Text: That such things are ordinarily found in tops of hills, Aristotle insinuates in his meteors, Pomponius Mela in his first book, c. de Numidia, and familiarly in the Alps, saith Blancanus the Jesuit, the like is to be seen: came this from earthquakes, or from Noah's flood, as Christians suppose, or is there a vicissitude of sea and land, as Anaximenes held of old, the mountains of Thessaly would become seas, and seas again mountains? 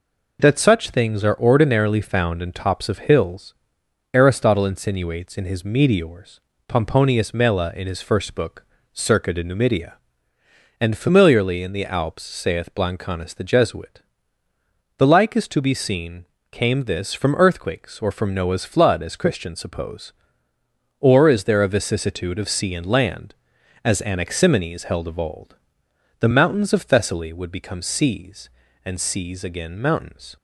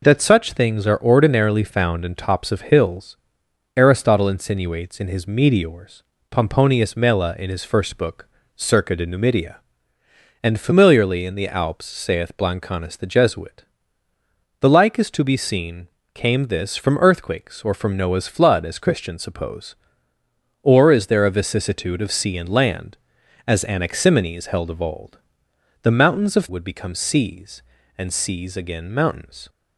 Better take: first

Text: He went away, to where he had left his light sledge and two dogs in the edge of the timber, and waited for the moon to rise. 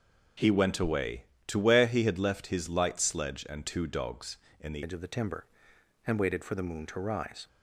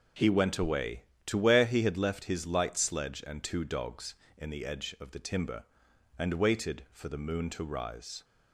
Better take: second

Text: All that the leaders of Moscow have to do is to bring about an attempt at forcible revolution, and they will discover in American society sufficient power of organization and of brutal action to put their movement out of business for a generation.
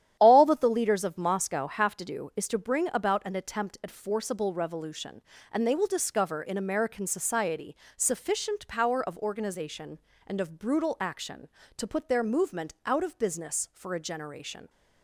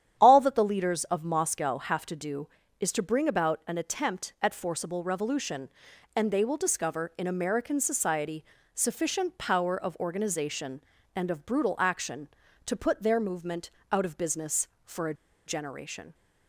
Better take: first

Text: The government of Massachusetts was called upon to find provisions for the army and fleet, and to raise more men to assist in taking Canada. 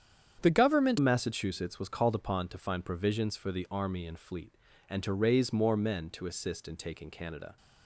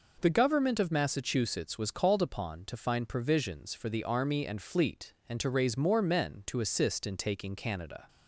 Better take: second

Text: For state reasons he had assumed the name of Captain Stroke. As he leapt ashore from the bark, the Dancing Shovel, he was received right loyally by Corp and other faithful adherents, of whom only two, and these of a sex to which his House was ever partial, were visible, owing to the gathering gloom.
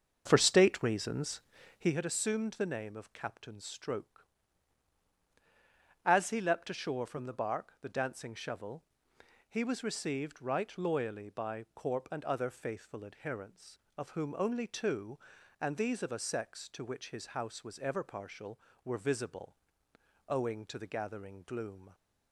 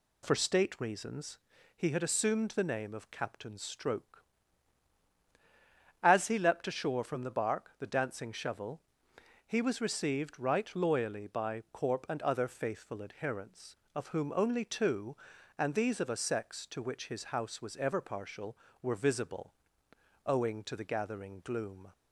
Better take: second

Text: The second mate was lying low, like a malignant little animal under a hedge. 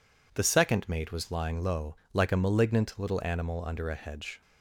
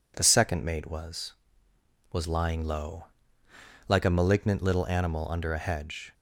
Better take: first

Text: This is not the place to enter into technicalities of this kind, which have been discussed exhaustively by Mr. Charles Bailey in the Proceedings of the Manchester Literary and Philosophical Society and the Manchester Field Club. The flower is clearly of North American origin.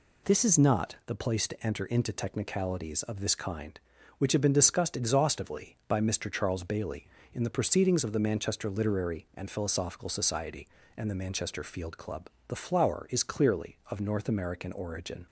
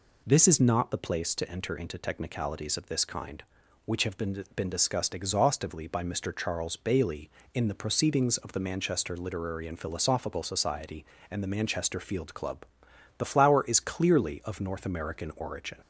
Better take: first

